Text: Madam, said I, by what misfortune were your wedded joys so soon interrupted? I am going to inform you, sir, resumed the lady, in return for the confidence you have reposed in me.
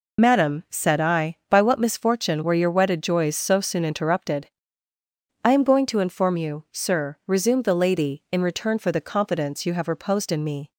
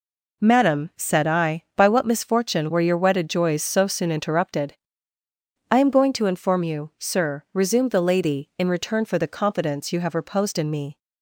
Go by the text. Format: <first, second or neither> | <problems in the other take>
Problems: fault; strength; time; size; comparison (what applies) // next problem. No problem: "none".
second | loses the start of "Madam"; at 0.1 s; 50 ms